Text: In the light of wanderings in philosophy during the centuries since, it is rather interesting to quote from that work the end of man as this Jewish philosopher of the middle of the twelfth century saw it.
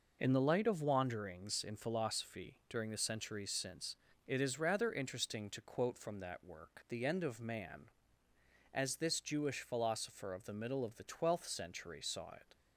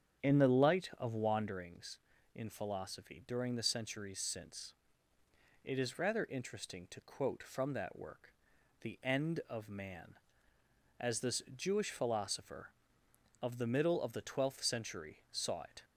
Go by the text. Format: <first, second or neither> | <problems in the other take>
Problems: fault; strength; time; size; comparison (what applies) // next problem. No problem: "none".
first | starts louder than the rest; strong; until 1.7 s; 8.5 dB // pauses between "work" and "the"; noticeable; at 8.3 s; 0.48 s long